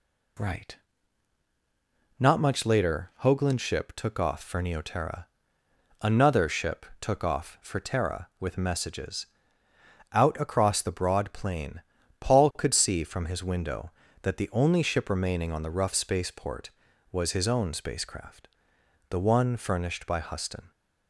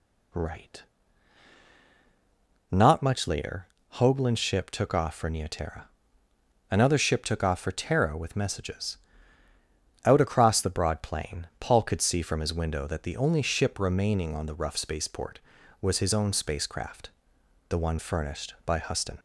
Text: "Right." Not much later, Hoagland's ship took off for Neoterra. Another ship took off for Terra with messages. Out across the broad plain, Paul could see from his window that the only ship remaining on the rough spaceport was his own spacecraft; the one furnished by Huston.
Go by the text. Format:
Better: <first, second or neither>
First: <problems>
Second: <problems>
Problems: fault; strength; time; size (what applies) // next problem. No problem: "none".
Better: neither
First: none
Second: none